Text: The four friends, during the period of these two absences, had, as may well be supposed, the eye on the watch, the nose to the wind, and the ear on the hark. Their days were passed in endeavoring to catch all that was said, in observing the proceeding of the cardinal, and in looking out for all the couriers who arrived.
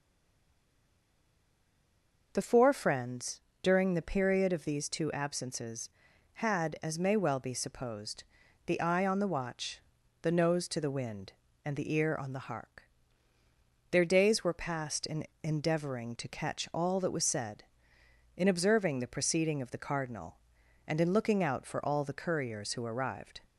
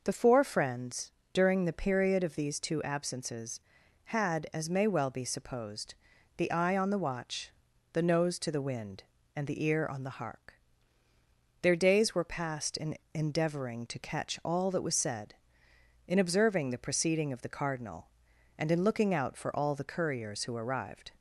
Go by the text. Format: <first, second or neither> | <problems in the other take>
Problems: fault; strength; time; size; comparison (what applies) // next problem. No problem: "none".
second | stays silent before the first word; until 2.3 s; 2.3 s long // pauses between "in" and "endeavoring"; slight; at 15.2 s; 0.16 s long; slight in the second